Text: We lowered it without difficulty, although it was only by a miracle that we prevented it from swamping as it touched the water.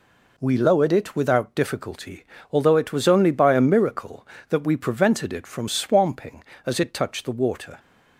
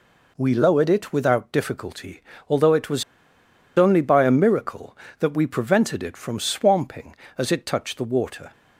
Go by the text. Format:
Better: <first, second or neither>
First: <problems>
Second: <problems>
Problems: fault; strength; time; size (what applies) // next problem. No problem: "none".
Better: first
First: none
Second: pauses between "was" and "only"; noticeable; at 3.0 s; 0.73 s long